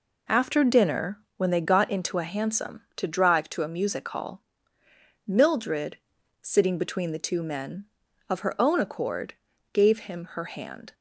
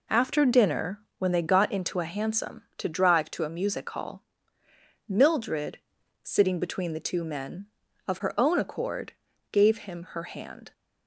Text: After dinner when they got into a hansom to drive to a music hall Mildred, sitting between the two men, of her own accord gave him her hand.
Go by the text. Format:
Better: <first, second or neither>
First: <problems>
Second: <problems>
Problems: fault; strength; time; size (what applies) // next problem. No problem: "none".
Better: neither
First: pauses between "dinner" and "when"; slight; at 1.1 s; 0.18 s long // pauses between "hall" and "Mildred"; noticeable; at 4.4 s; 0.86 s long // pauses between "accord" and "gave"; at 9.3 s; 0.40 s long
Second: pauses between "dinner" and "when"; slight; at 0.9 s; 0.18 s long // pauses between "hall" and "Mildred"; noticeable; at 4.2 s; 0.86 s long // pauses between "accord" and "gave"; at 9.1 s; 0.40 s long